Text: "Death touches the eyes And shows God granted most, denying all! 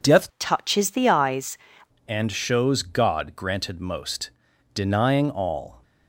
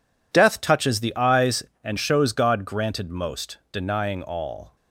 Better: second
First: changes voice from "touches" to "eyes"; from 0.3 to 1.5 s; 1.2 s long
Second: none

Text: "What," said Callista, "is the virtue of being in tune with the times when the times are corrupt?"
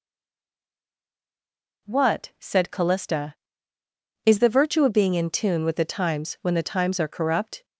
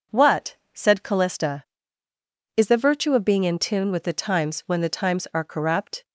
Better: second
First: stays silent before the first word; noticeable; until 1.8 s; 1.8 s long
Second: none

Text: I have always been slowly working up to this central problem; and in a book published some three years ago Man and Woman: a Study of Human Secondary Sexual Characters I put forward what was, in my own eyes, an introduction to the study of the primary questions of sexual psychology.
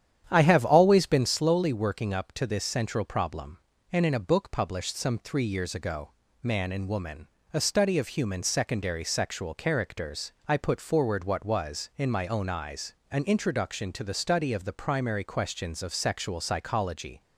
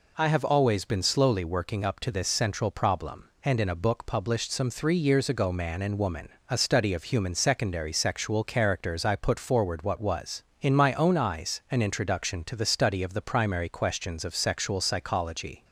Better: second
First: starts louder than the rest; strong; until 1.3 s; 9.5 dB // pauses between "ago" and "Man"; slight; at 6.1 s; 0.28 s long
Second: none

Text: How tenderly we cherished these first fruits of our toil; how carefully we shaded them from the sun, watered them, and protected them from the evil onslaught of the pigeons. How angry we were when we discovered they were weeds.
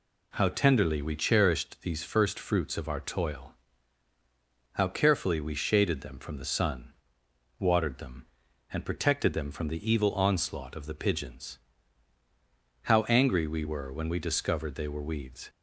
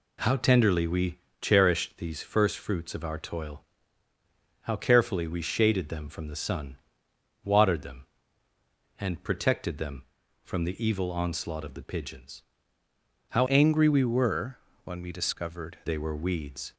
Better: first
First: none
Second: pauses between "we" and "cherished"; slight; at 1.1 s; 0.20 s long // changes voice from "angry" to "discovered"; from 13.4 to 15.7 s; 2.3 s long // pauses between "were" and "when"; slight; at 14.5 s; 0.28 s long

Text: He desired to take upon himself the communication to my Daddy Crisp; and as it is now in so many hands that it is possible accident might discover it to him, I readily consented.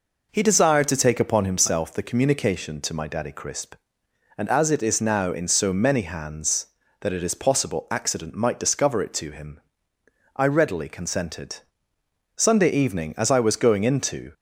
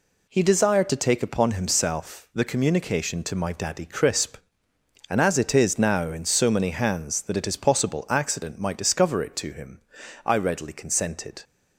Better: second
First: goes on to say "Sunday evening as I was going into"; strong; from 12.3 s on; 1.9 s long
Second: none

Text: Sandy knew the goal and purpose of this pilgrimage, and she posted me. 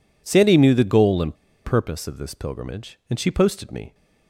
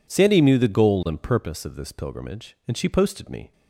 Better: second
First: pauses between "and" and "purpose"; slight; at 1.3 s; 0.28 s long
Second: none

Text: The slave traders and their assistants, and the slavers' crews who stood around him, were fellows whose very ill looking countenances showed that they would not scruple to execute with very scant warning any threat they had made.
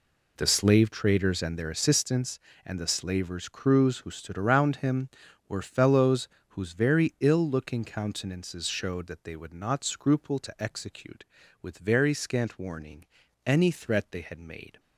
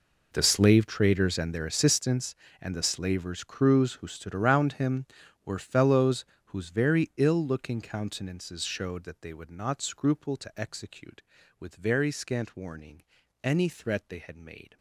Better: first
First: pauses between "fellows" and "whose"; slight; at 6.2 s; 0.22 s long // pauses between "warning" and "any"; at 13.0 s; 0.40 s long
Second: gets quieter; strong; throughout; 17.5 dB // pauses between "fellows" and "whose"; slight; at 6.2 s; 0.22 s long // pauses between "warning" and "any"; at 13.0 s; 0.40 s long

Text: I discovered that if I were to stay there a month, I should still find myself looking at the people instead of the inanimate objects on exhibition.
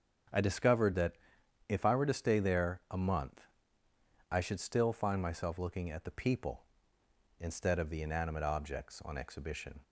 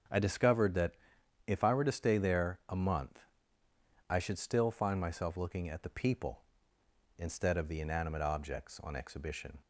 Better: neither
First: starts louder than the rest; strong; until 1.9 s; 8 dB // pauses between "that" and "if"; noticeable; at 1.1 s; 0.54 s long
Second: starts louder than the rest; strong; until 1.6 s; 7.5 dB // pauses between "that" and "if"; noticeable; at 0.9 s; 0.53 s long

